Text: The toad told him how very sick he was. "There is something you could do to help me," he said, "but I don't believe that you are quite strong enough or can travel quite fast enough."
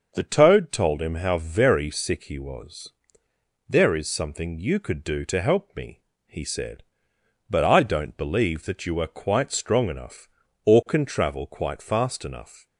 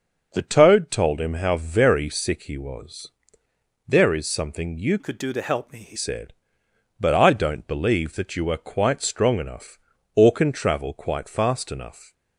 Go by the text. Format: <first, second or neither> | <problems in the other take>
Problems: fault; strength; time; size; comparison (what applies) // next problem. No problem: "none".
first | starts louder than the rest; noticeable; until 1.3 s; 6 dB // changes voice from "could" to "he"; from 4.9 to 5.9 s; 1.0 s long